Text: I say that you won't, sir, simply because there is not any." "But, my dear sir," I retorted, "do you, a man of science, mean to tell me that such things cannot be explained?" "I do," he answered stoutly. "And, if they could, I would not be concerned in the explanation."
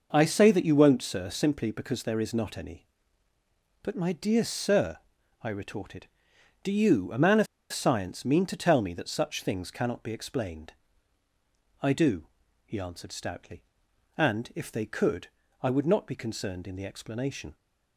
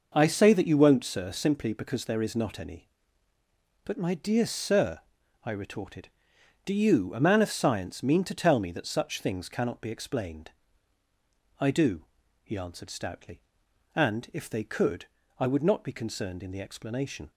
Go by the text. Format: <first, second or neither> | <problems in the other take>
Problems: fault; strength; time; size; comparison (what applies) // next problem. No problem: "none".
second | pauses between "of" and "science"; slight; at 7.4 s; 0.26 s long